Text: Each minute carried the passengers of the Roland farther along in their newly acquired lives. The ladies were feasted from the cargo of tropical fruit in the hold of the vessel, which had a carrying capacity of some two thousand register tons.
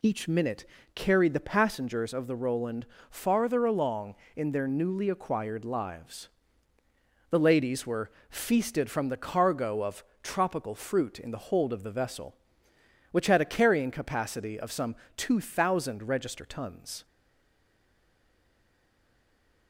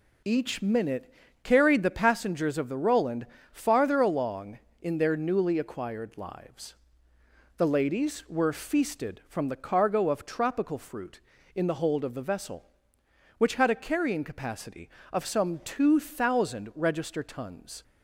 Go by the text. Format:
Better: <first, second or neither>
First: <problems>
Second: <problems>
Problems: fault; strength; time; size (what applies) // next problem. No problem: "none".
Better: second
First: pauses between "minute" and "carried"; slight; at 0.6 s; 0.30 s long // pauses between "Roland" and "farther"; slight; at 2.8 s; 0.24 s long // pauses between "were" and "feasted"; slight; at 8.1 s; 0.18 s long // pauses between "of" and "tropical"; slight; at 10.0 s; 0.20 s long // pauses between "some" and "two"; slight; at 14.9 s; 0.22 s long // stays silent after the last word; strong; from 17.0 s on; 2.6 s long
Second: pauses between "minute" and "carried"; slight; at 1.1 s; 0.30 s long // pauses between "Roland" and "farther"; slight; at 3.2 s; 0.26 s long